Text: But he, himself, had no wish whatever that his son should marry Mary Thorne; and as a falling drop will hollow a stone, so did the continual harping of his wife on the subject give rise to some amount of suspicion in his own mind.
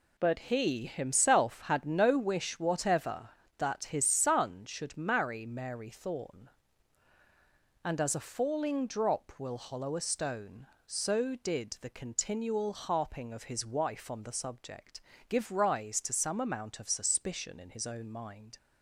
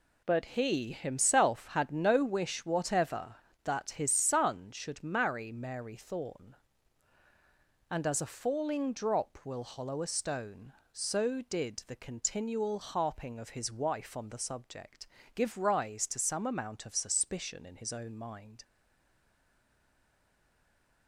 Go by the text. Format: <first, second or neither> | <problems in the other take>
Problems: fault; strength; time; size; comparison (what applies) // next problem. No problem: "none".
first | pauses between "subject" and "give"; slight; at 15.0 s; 0.28 s long; slight in the first // stays silent after the last word; from 18.6 s on; 2.4 s long